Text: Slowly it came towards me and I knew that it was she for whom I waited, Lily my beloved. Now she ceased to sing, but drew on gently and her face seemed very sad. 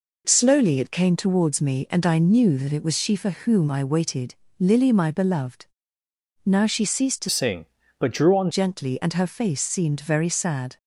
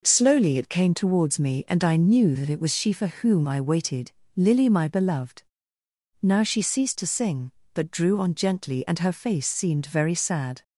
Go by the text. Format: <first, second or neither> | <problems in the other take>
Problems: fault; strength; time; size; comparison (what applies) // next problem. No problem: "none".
second | changes voice from "sing" to "on"; from 7.2 to 8.5 s; 1.3 s long